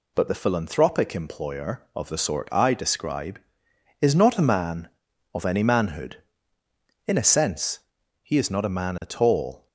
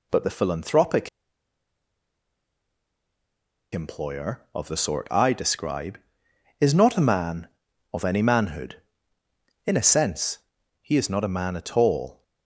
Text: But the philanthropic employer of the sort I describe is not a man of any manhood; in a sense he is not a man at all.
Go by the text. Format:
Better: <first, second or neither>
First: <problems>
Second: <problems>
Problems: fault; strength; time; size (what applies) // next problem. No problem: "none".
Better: first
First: pauses between "sense" and "he"; at 7.7 s; 0.42 s long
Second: pauses between "philanthropic" and "employer"; strong; at 1.0 s; 2.6 s long // pauses between "sense" and "he"; at 10.3 s; 0.42 s long